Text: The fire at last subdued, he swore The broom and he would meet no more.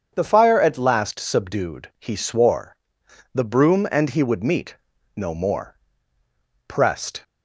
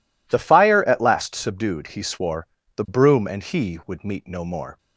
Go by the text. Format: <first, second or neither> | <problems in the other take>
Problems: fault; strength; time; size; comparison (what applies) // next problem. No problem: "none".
second | starts louder than the rest; strong; until 1.1 s; 7 dB // pauses between "swore" and "The"; noticeable; at 2.7 s; 0.58 s long; slight in the second // pauses between "meet" and "no"; at 4.7 s; 0.40 s long // goes on to say "Pressed"; from 6.6 s on; 0.56 s long